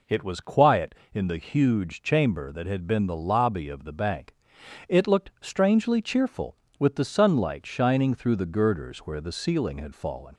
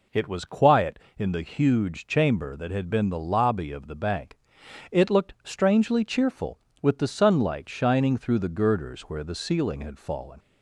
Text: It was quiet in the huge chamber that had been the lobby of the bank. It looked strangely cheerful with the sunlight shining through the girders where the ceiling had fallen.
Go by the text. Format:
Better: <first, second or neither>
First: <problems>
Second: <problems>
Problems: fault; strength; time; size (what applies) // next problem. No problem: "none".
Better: neither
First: none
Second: none